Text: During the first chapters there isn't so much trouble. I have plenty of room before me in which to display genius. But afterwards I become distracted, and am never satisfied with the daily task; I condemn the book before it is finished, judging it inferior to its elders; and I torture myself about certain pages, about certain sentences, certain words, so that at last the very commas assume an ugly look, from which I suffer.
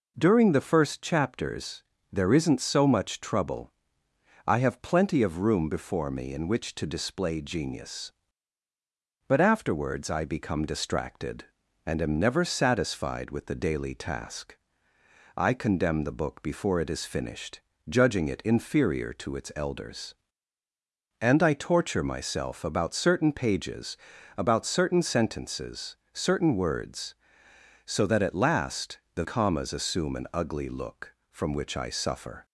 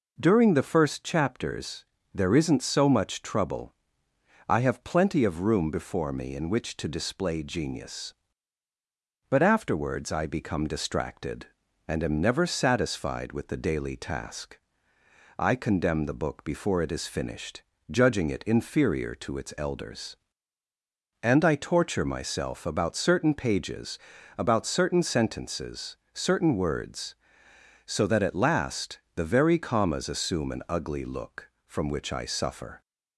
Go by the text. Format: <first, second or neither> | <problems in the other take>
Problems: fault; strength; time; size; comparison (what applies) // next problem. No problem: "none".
second | pauses between "chapters" and "there"; slight; at 1.8 s; 0.30 s long; slight in the second // skips "very"; at 29.2 s